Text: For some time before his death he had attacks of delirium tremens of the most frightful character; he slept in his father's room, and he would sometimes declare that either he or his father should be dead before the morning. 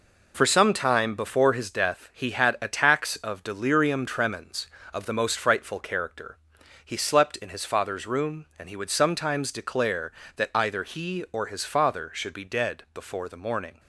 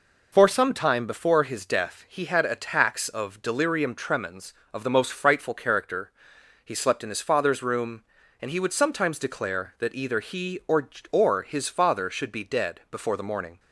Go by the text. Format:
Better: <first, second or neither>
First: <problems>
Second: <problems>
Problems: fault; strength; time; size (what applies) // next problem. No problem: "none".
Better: first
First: none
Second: says "or" twice; at 11.1 s